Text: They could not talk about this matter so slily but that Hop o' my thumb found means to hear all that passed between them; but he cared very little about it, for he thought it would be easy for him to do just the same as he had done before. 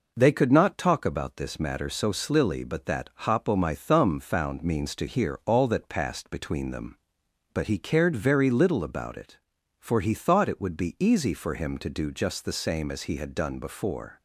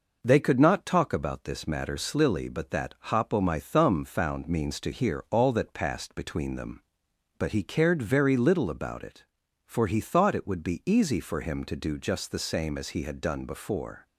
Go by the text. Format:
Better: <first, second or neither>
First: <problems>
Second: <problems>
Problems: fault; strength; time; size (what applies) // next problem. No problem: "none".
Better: first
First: pauses between "that" and "Hop"; slight; at 3.0 s; 0.16 s long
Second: skips "so"; at 1.9 s // pauses between "that" and "Hop"; slight; at 2.9 s; 0.16 s long